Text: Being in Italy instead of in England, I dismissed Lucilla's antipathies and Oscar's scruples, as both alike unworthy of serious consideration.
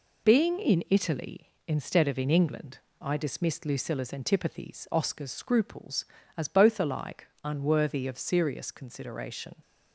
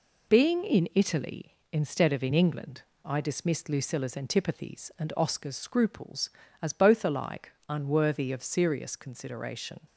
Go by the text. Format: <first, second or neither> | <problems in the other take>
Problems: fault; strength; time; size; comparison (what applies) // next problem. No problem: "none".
second | skips "and"; at 4.8 s // pauses between "alike" and "unworthy"; slight; at 7.2 s; 0.16 s long; slight in the second